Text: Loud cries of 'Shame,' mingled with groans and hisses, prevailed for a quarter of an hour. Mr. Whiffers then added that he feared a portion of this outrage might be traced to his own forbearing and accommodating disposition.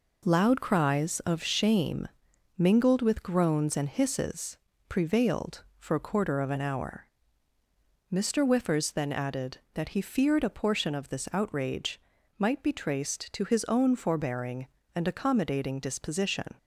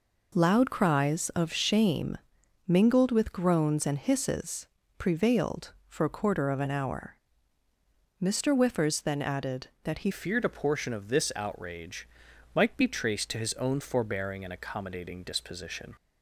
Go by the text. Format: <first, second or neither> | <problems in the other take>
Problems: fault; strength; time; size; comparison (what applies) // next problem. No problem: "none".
first | changes voice at "feared"; from 10.1 s on; 5.8 s long // pauses between "outrage" and "might"; noticeable; at 12.0 s; 0.48 s long; also in the first